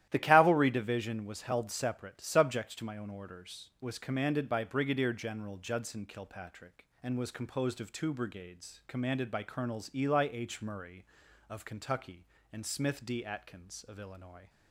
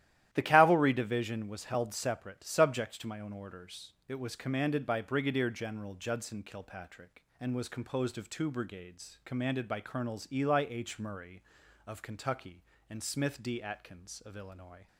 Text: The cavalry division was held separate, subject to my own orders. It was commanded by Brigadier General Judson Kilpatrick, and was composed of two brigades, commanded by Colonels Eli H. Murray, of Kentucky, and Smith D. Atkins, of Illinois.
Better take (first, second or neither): second